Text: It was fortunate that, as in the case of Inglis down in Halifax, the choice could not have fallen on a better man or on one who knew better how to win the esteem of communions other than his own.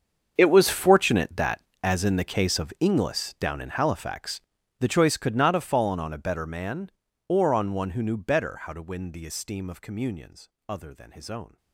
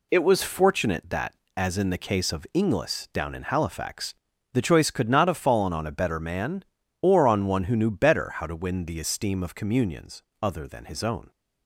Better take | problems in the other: second | gets quieter; strong; throughout; 18.5 dB // pauses between "communions" and "other"; slight; at 10.4 s; 0.20 s long; slight in the second

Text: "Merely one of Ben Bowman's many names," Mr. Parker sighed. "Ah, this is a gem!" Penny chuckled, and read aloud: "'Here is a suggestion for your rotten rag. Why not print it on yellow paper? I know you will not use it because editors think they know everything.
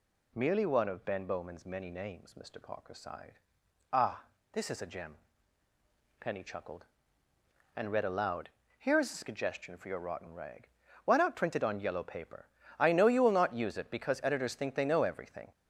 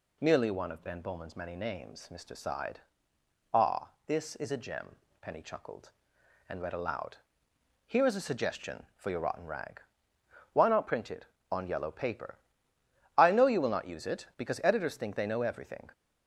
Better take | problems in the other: first | skips "Parker"; at 2.3 s

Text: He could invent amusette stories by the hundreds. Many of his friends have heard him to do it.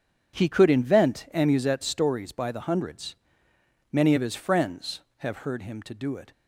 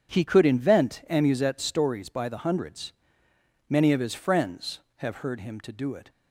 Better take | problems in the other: neither | none

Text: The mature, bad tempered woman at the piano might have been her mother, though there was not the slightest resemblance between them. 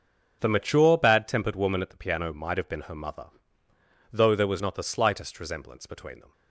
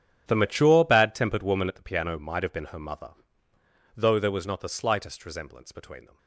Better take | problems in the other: first | gets quieter; strong; throughout; 17.5 dB // starts louder than the rest; strong; until 1.2 s; 10.5 dB; also in the first

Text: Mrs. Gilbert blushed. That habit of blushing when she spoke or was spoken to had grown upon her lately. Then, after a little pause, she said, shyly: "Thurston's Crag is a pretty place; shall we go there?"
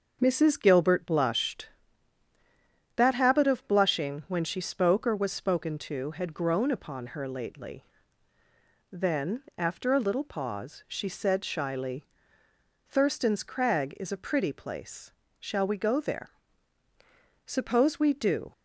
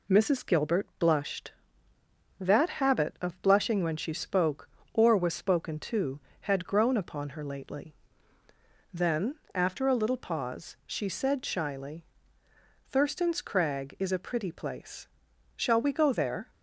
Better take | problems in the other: second | starts louder than the rest; until 1.2 s; 6.5 dB // goes on to say "Suppose we do"; noticeable; from 17.4 s on; 1.0 s long

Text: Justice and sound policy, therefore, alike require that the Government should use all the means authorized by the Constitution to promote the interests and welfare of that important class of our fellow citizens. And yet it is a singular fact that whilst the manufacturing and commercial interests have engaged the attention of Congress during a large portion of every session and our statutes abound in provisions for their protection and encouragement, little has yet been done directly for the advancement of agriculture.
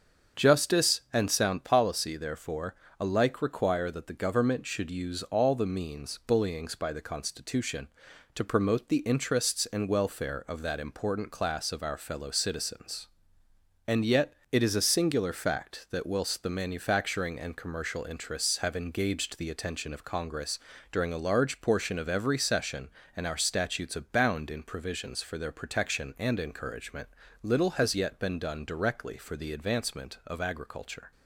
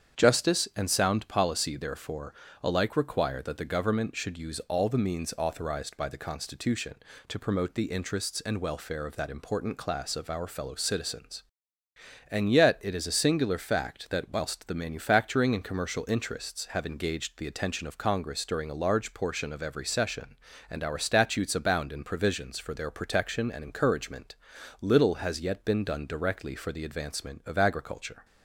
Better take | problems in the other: second | starts louder than the rest; strong; until 1.4 s; 7.5 dB; strong in the second // says "bullyings" for "authorized"; at 6.2 s // pauses between "yet" and "it"; slight; at 14.3 s; 0.18 s long // pauses between "Congress" and "during"; slight; at 20.5 s; 0.34 s long

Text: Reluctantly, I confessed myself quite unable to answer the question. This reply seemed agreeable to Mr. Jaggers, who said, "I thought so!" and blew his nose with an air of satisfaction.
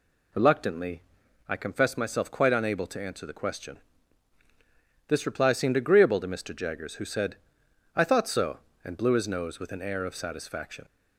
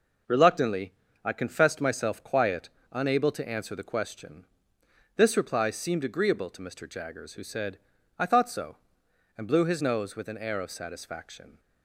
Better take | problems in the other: first | says "quiet" for "quite"; at 2.2 s

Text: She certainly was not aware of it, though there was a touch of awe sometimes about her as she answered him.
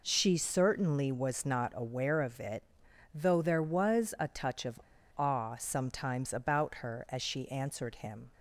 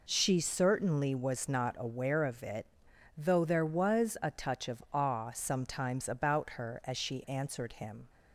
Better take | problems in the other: second | pauses between "of" and "awe"; at 4.7 s; 0.39 s long

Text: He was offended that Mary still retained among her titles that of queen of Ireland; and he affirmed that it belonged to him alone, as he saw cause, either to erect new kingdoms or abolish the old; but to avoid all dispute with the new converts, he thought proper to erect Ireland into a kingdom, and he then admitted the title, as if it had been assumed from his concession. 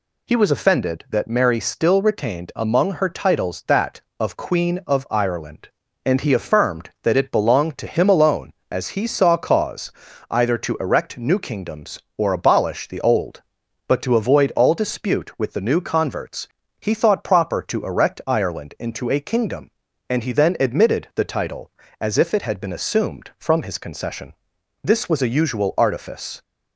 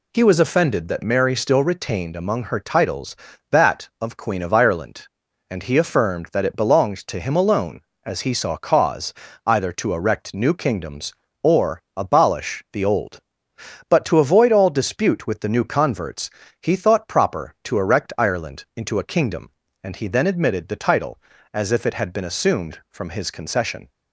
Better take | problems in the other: second | goes on to say "This was a usual artifice"; from 24.8 s on; 1.5 s long

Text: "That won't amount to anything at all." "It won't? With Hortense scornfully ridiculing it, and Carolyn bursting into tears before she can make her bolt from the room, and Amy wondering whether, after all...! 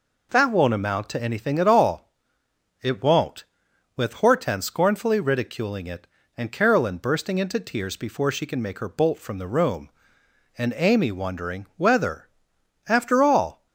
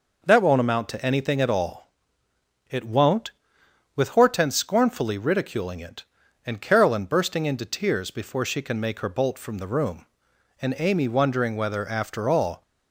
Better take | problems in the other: neither | none

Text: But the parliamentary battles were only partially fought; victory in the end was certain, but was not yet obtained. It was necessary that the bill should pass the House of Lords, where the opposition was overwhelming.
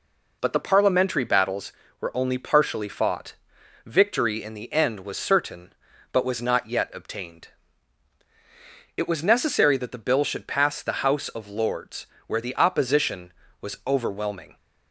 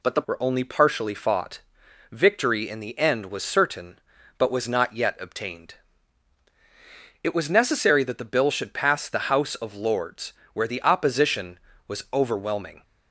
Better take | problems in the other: first | skips "parliamentary battles"; at 0.2 s

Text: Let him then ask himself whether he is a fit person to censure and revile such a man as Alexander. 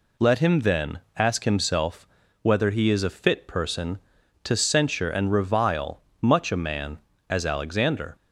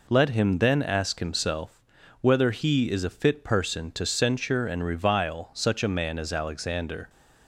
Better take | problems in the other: second | pauses between "then" and "ask"; slight; at 0.9 s; 0.18 s long // pauses between "himself" and "whether"; slight; at 2.0 s; 0.34 s long; also in the second // says "much" for "such"; at 6.2 s

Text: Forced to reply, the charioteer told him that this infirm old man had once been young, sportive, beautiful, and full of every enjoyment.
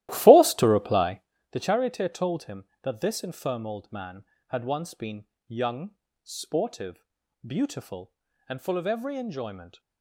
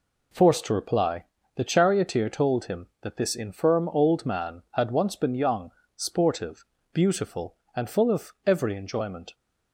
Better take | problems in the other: second | starts louder than the rest; strong; until 1.4 s; 15 dB // pauses between "been" and "young"; slight; at 5.2 s; 0.24 s long

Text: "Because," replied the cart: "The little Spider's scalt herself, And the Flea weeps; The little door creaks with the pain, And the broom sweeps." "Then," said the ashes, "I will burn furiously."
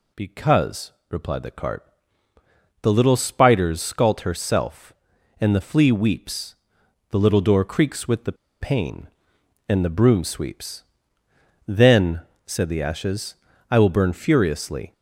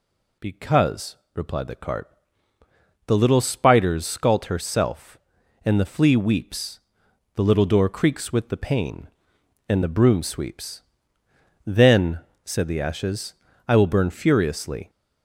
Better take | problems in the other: second | pauses between "the" and "pain"; slight; at 8.3 s; 0.27 s long

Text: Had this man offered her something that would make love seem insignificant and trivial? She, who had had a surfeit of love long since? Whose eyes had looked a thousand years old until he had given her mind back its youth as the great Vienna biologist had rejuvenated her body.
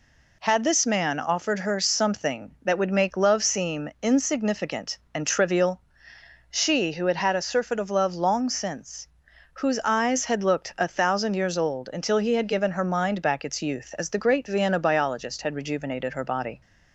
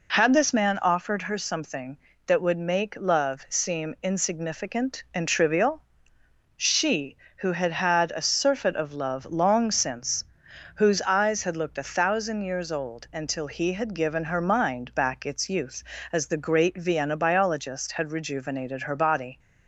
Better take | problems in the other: neither | none

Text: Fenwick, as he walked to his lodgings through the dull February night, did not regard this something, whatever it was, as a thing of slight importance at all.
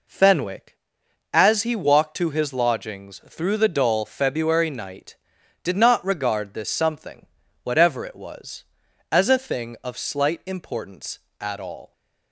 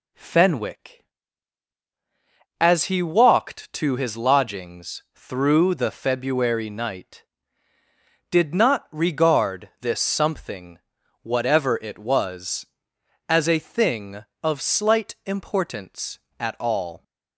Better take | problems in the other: first | skips "dull"; at 5.9 s

